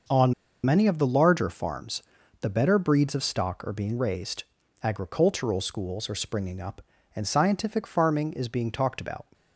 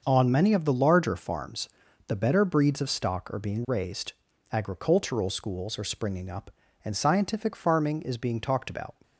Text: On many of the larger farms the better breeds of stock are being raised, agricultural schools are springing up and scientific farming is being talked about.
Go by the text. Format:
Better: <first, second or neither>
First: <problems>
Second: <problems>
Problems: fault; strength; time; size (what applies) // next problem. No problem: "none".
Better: second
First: starts louder than the rest; noticeable; until 1.4 s; 6 dB // pauses between "On" and "many"; slight; at 0.3 s; 0.30 s long // pauses between "farms" and "the"; at 2.0 s; 0.38 s long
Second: starts louder than the rest; until 1.0 s; 6 dB // pauses between "farms" and "the"; at 1.6 s; 0.38 s long